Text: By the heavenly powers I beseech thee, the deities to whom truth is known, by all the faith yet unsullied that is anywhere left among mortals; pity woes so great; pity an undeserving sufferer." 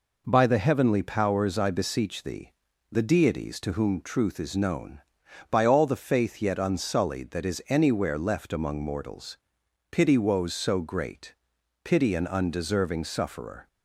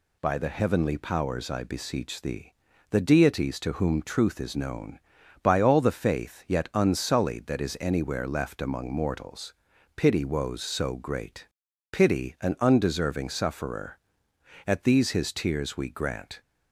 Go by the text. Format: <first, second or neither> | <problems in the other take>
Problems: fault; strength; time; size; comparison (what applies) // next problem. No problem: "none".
first | goes on to say "At these his tears we grant"; strong; from 14.6 s on; 1.7 s long